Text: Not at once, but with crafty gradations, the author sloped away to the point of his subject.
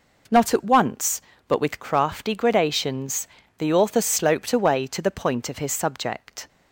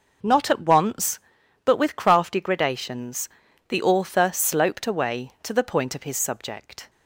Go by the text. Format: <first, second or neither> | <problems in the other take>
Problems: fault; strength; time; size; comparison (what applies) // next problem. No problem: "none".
neither | none